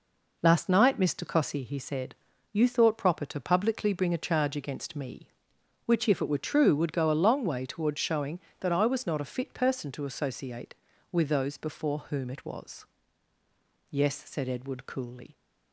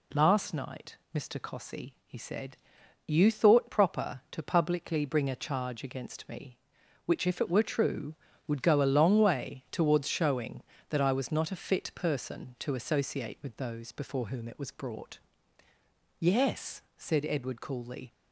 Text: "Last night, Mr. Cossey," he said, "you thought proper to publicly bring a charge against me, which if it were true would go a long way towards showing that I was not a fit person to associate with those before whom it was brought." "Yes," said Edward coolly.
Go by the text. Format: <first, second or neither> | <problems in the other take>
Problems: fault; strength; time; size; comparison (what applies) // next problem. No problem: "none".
second | skips "brought"; at 13.3 s